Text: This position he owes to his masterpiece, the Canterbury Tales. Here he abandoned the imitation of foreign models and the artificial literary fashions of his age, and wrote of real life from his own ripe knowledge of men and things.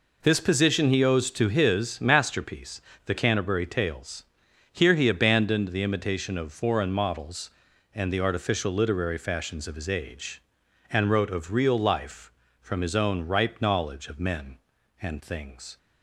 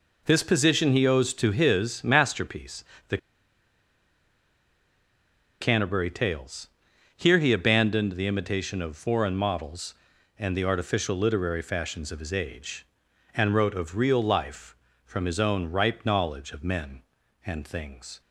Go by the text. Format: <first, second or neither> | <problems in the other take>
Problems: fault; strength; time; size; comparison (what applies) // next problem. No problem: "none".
first | pauses between "the" and "Canterbury"; strong; at 3.1 s; 2.4 s long